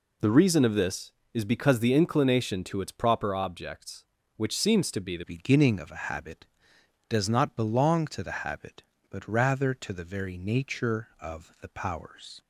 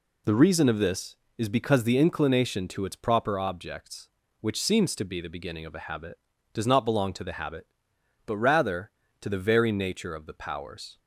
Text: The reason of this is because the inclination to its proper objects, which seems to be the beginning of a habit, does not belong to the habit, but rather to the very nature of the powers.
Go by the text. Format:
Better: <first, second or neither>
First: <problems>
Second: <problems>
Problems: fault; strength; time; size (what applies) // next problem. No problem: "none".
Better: second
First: changes voice at "beginning"; from 5.2 s on; 7.2 s long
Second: none